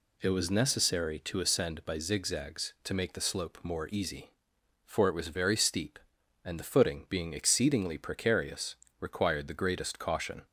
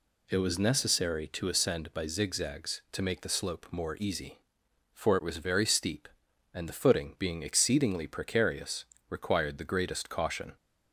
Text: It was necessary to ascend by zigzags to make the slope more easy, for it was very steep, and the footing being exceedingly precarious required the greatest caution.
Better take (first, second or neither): neither